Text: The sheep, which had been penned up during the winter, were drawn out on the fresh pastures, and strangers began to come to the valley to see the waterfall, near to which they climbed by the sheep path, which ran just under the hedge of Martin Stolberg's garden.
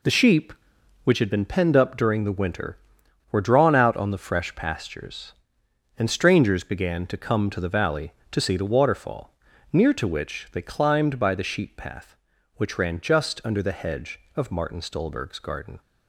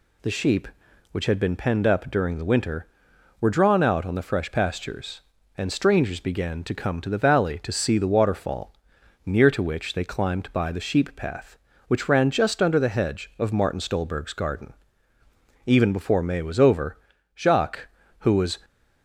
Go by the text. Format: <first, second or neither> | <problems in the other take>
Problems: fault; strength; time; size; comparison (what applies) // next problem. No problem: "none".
first | goes on to say "Even before May was over Jacques who was"; strong; from 15.6 s on; 2.9 s long